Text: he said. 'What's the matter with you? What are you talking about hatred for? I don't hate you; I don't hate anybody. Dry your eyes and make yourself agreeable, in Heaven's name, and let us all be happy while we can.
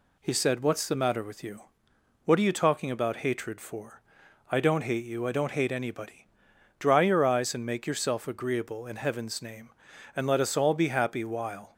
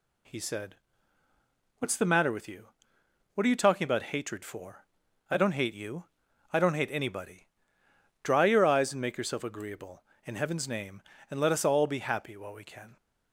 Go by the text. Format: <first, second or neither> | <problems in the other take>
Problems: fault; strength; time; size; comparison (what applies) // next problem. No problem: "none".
second | stops before "we can"; at 11.7 s